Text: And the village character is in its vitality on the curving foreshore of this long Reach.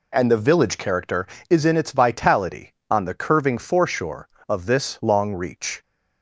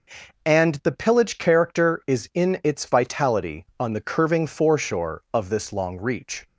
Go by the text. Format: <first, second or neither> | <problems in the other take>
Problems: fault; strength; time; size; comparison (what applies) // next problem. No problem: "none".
first | says "pillage" for "village"; at 0.9 s